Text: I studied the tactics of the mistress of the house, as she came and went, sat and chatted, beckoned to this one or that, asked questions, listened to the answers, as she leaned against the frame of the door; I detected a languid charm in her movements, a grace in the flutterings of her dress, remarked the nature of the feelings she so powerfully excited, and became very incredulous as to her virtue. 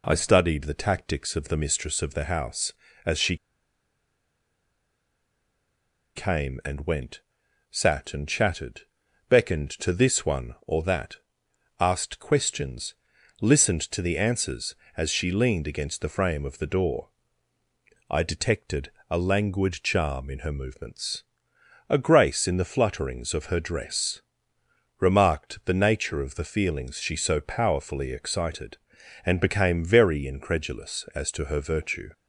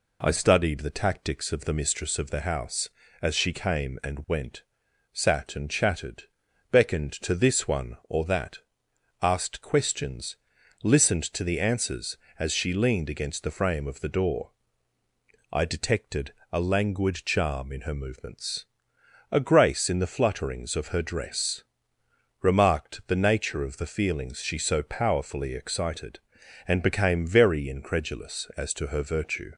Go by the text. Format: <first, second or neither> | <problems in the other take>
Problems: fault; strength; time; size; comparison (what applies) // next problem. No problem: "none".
second | pauses between "she" and "came"; strong; at 3.3 s; 2.8 s long // pauses between "detected" and "a"; slight; at 18.9 s; 0.18 s long; slight in the second